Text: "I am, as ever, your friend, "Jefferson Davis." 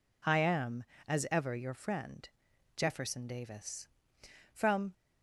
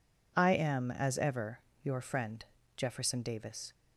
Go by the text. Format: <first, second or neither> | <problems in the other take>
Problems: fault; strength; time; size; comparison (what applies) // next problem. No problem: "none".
second | goes on to say "From"; slight; from 4.5 s on; 0.40 s long